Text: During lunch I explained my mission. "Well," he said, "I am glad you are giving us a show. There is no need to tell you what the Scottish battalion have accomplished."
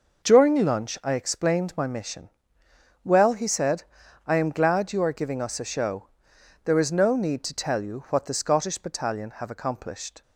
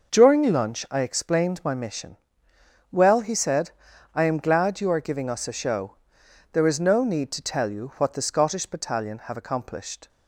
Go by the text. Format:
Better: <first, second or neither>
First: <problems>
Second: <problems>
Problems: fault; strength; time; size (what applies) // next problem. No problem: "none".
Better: neither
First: none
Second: none